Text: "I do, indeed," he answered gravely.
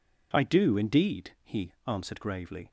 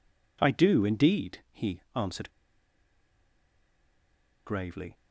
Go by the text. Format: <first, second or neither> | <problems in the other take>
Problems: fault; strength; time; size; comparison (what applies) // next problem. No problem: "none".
first | pauses between "answered" and "gravely"; strong; at 2.2 s; 2.1 s long